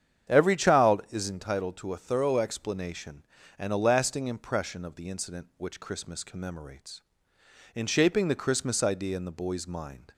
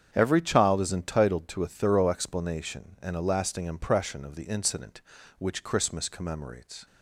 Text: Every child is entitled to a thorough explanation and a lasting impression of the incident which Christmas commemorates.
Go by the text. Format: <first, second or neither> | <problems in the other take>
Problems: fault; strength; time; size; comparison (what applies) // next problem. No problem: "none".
second | starts louder than the rest; strong; until 1.3 s; 8.5 dB; strong in the second // goes on to say "In shaping the Christmas idea in the boy's mind"; strong; from 7.7 s on; 2.3 s long